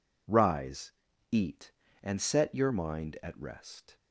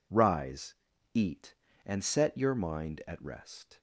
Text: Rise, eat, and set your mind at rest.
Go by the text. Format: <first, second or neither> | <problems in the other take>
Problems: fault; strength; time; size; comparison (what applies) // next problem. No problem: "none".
neither | none